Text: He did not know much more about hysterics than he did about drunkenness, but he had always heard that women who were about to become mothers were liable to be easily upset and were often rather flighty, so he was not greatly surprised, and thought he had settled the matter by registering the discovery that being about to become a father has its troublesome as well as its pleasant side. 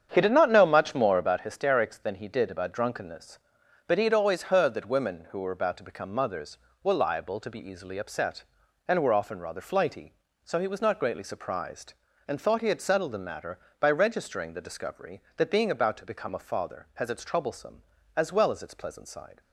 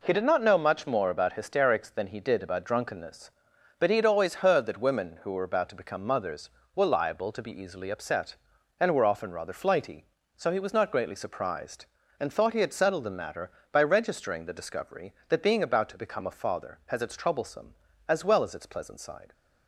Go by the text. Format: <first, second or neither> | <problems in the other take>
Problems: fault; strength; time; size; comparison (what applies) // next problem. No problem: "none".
second | starts louder than the rest; strong; until 1.4 s; 8 dB